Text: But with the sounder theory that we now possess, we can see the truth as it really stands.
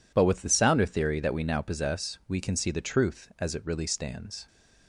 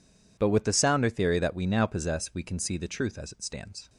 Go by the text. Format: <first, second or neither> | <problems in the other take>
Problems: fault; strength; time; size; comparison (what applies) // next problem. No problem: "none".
first | skips "really"; at 3.4 s